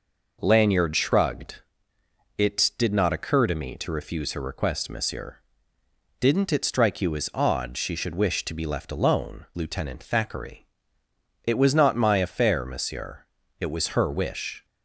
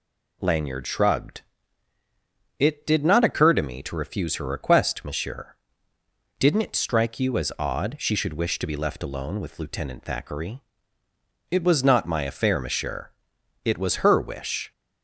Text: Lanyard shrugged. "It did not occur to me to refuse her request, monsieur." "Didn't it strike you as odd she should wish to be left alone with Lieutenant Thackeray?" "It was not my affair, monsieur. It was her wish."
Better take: second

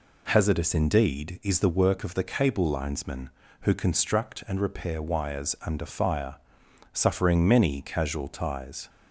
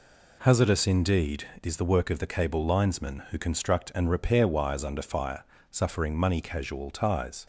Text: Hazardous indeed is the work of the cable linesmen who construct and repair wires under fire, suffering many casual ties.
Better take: first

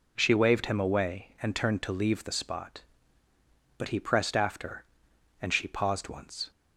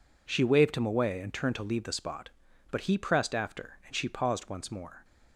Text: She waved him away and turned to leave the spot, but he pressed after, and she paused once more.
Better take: second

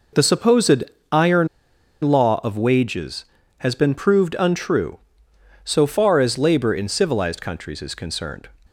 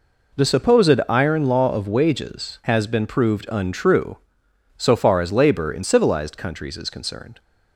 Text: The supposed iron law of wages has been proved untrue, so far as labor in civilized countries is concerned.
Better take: second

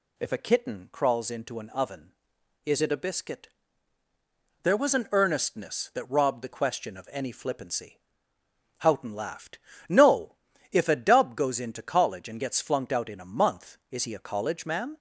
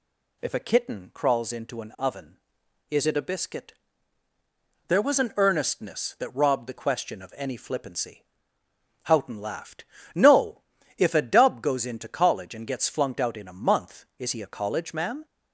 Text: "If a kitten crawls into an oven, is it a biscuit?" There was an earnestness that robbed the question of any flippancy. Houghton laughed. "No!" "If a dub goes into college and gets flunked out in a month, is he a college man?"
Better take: neither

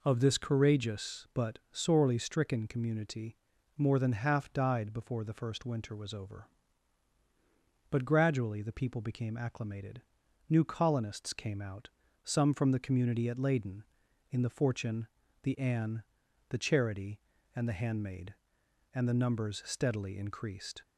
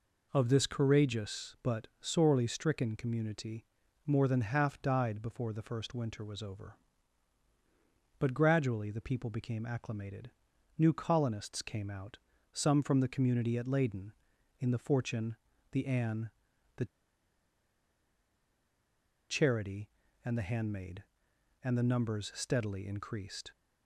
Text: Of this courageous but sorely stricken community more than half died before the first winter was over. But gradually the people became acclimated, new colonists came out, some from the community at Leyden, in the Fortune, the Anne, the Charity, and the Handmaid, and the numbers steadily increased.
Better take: first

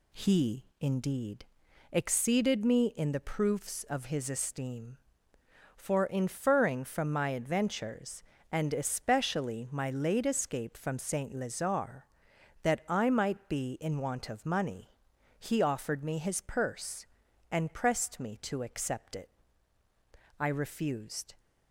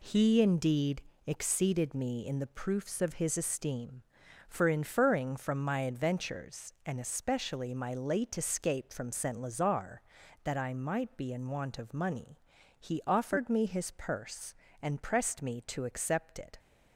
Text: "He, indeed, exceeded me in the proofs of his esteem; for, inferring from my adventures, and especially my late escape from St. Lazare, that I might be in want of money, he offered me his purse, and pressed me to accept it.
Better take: second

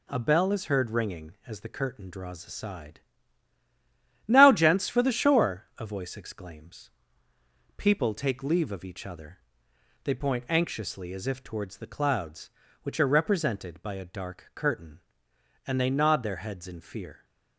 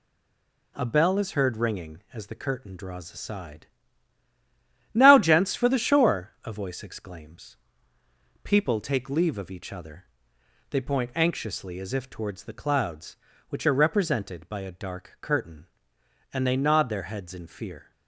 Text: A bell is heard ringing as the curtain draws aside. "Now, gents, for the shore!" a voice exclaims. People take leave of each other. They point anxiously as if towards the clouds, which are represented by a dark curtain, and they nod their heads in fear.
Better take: first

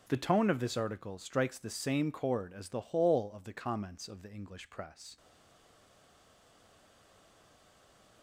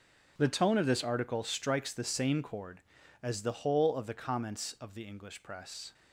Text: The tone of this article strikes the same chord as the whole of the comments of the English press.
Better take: second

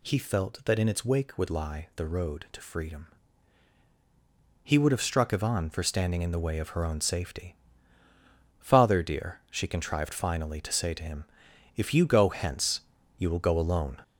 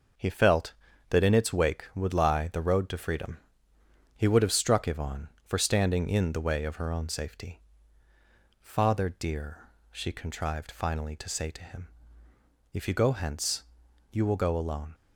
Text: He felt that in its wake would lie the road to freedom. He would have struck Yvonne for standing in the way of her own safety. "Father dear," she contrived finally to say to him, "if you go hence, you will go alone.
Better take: second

